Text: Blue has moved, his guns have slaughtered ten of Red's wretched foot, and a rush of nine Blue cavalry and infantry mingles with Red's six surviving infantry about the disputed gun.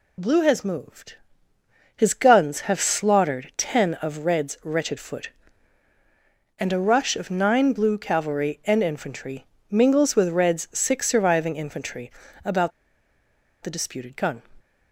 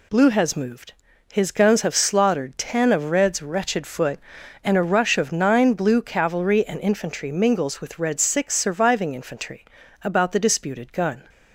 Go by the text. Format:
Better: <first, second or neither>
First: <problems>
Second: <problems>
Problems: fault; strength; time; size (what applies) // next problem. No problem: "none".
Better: second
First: pauses between "infantry" and "mingles"; slight; at 9.4 s; 0.26 s long // pauses between "infantry" and "about"; slight; at 12.1 s; 0.32 s long // pauses between "about" and "the"; noticeable; at 12.7 s; 0.93 s long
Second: pauses between "infantry" and "about"; at 9.6 s; 0.38 s long